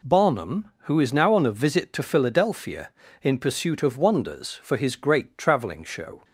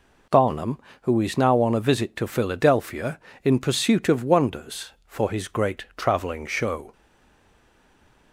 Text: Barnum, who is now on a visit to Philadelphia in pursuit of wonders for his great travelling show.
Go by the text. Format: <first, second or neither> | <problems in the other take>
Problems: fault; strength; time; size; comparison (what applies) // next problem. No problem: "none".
first | stays silent after the last word; noticeable; from 6.9 s on; 1.4 s long